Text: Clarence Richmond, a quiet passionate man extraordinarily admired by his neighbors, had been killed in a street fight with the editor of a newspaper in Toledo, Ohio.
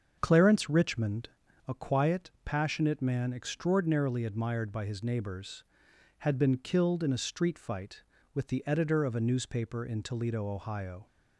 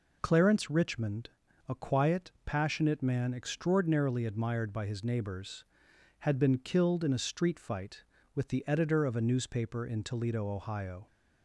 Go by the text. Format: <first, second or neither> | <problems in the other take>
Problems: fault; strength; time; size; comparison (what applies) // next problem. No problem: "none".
second | starts louder than the rest; until 1.7 s; 7 dB